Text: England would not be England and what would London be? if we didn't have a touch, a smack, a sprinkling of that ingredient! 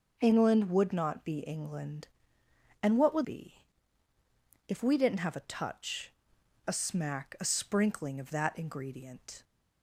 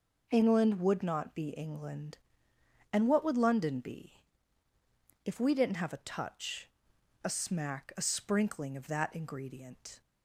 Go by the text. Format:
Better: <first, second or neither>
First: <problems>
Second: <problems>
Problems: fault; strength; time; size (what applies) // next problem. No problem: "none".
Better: second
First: starts louder than the rest; until 1.2 s; 6 dB // skips "London"; at 3.2 s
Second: none